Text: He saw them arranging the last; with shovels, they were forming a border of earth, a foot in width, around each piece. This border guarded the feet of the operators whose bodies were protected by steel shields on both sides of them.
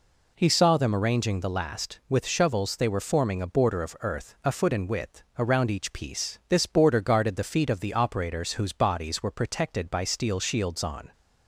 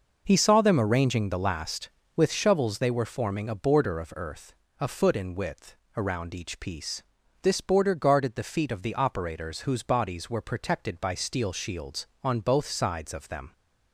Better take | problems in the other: second | stops before "both sides of them"; at 11.1 s

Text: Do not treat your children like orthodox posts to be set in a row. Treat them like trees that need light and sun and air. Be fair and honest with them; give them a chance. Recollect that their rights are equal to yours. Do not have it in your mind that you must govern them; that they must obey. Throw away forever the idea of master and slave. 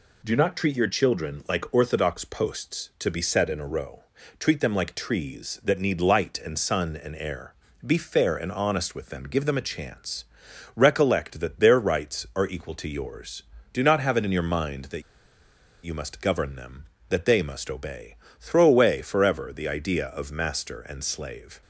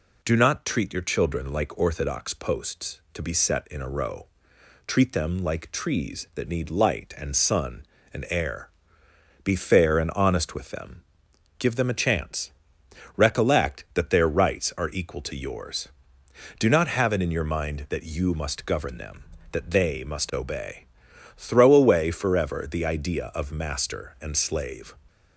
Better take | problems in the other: second | pauses between "that" and "you"; noticeable; at 15.0 s; 0.80 s long

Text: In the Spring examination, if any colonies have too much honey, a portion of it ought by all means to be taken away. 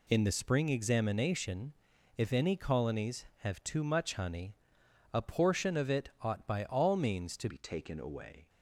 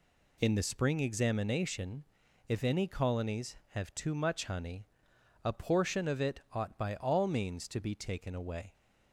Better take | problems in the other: second | changes voice at "be"; from 7.4 s on; 1.0 s long

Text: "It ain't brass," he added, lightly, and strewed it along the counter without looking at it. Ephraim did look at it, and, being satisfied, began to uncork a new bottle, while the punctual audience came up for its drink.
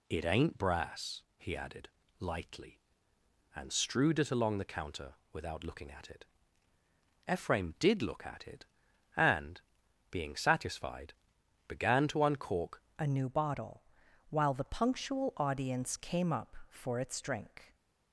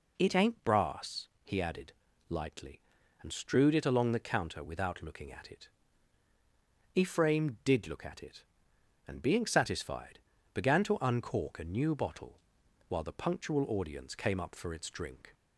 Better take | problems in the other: second | pauses between "counter" and "without"; slight; at 5.1 s; 0.16 s long // changes voice at "a"; from 12.9 s on; 4.8 s long

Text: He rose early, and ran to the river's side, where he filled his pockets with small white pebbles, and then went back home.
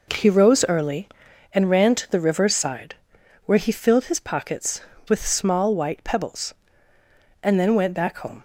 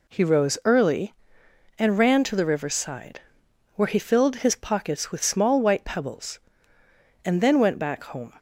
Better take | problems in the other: neither | none

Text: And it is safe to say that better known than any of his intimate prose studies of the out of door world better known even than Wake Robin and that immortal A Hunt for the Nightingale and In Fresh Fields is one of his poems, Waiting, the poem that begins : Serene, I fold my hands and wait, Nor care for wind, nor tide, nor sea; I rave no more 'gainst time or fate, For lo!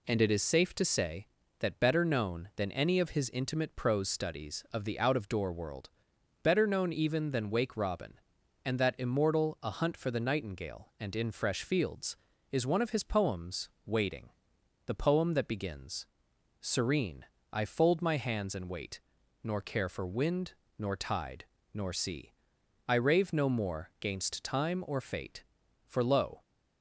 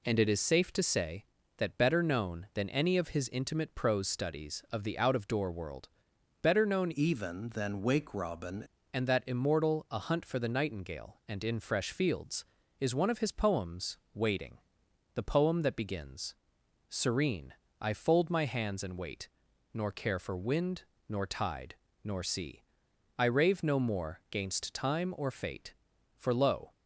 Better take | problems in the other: first | pauses between "world" and "better"; noticeable; at 5.8 s; 0.52 s long; noticeable in the first // changes voice from "even" to "Robin"; from 6.9 to 8.6 s; 1.7 s long

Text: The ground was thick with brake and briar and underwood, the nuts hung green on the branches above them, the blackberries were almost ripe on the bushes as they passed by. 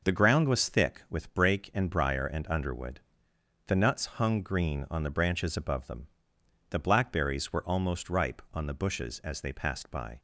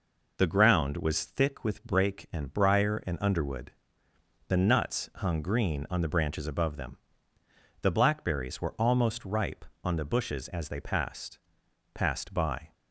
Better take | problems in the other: first | says "passed" twice; at 11.9 s

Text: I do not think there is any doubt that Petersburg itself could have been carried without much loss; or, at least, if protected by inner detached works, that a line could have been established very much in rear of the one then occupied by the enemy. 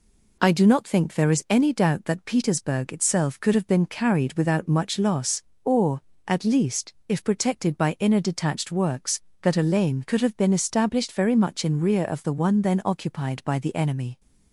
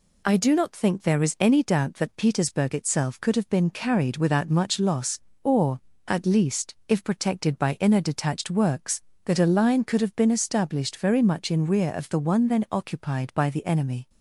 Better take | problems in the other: second | says "lane" for "line"; at 9.6 s

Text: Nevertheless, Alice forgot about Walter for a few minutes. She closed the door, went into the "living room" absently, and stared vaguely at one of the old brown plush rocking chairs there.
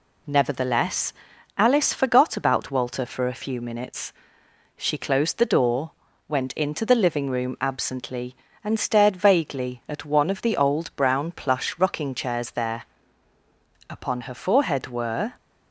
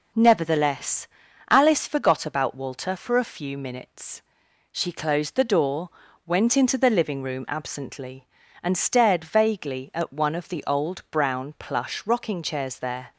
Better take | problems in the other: second | goes on to say "Upon her forehead were"; from 13.8 s on; 1.4 s long

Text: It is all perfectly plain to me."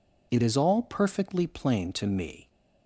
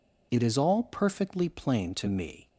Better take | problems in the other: neither | none

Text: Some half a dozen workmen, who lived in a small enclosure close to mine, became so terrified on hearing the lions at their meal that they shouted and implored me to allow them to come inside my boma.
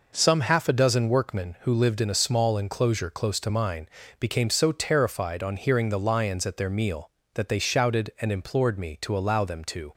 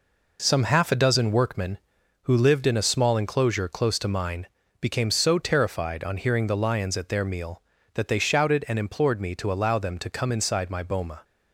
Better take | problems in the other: second | stops before "come inside my boma"; at 9.9 s

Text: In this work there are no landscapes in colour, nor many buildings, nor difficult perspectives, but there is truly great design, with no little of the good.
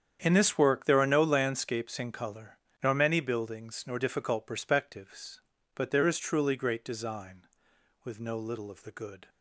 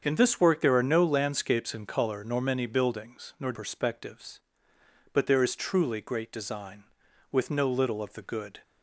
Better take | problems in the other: first | starts louder than the rest; strong; until 1.0 s; 7 dB; strong in the first // skips "difficult"; at 3.5 s

